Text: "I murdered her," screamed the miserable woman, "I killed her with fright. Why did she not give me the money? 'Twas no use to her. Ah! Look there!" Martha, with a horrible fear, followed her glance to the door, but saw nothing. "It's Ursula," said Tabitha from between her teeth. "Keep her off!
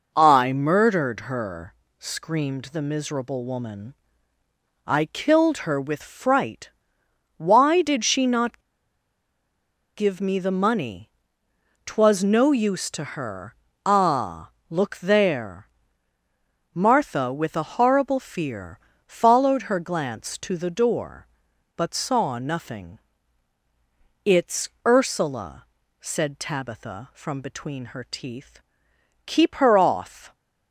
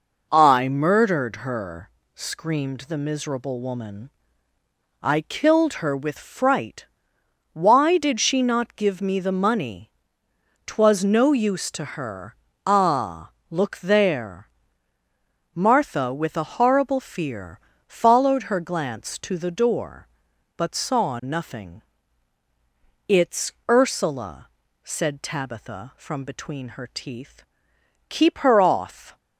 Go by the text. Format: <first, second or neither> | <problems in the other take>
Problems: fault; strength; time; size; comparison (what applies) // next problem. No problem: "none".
second | pauses between "not" and "give"; strong; at 8.6 s; 1.3 s long // pauses between "It's" and "Ursula"; slight; at 24.6 s; 0.18 s long; slight in the second